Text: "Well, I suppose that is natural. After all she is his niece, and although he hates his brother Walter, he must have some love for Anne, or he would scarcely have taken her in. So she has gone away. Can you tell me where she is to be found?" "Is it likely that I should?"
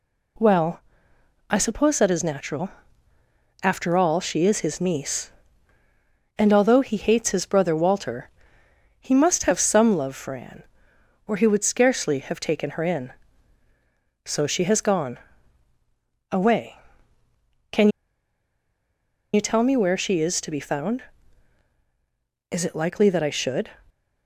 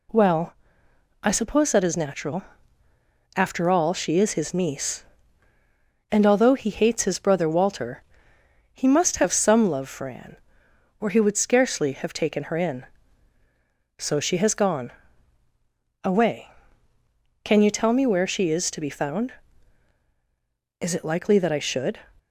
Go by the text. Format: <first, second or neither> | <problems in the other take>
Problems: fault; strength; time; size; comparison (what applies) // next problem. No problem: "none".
second | pauses between "gone" and "away"; at 15.1 s; 1.1 s long; also in the second // pauses between "Can" and "you"; strong; at 17.8 s; 1.4 s long